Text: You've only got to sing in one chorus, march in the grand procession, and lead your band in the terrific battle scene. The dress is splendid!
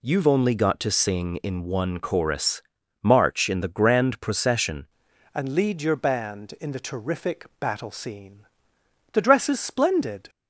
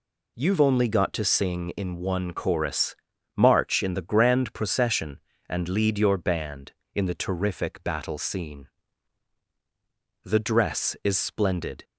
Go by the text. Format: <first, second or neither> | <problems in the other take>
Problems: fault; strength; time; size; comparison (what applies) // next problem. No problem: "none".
second | changes voice at "and"; from 5.3 s on; 4.9 s long